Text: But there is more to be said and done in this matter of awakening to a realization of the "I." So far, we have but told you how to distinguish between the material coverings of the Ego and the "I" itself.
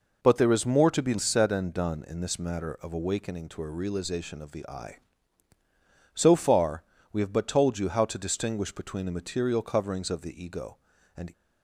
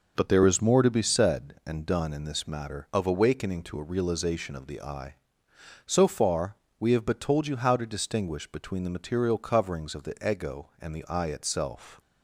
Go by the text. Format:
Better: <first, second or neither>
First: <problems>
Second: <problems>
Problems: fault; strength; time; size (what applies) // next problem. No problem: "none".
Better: second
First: stops before "the I itself"; at 11.3 s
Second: none